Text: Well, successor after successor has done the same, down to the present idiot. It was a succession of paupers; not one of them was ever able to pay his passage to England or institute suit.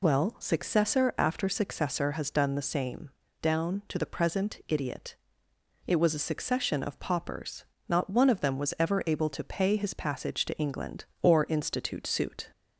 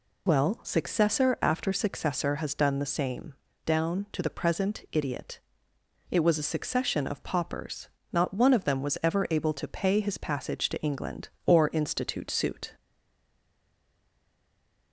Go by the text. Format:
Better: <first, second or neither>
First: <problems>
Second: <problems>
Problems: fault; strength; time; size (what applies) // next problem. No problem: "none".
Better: first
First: none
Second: stays silent after the last word; from 12.7 s on; 2.2 s long